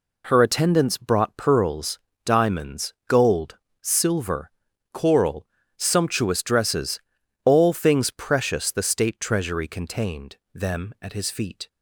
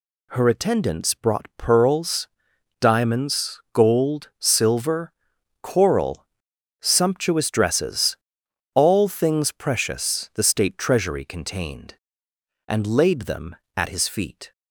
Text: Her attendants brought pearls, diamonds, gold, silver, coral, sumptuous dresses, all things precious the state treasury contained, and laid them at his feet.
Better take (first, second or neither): second